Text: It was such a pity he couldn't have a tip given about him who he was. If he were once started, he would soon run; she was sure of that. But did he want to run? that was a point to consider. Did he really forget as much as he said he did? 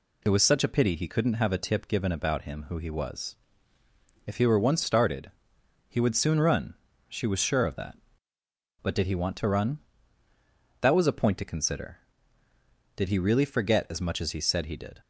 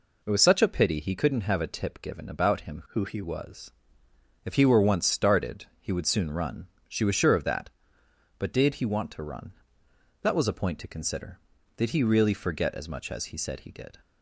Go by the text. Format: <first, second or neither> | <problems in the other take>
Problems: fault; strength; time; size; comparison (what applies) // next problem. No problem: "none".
first | changes voice from "who" to "he"; from 2.8 to 3.2 s; 0.4 s long